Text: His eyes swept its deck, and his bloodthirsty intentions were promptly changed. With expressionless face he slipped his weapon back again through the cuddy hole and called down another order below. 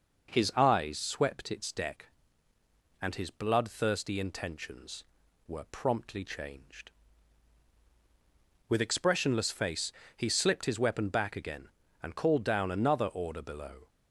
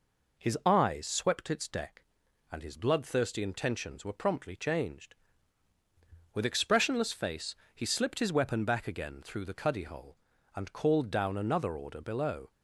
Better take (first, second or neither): second